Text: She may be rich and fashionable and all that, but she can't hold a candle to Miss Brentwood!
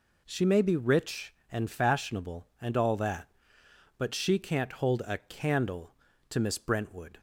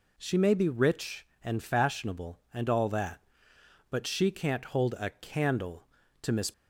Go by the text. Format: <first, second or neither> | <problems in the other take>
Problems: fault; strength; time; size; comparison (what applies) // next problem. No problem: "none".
first | stops before "Brentwood"; at 6.5 s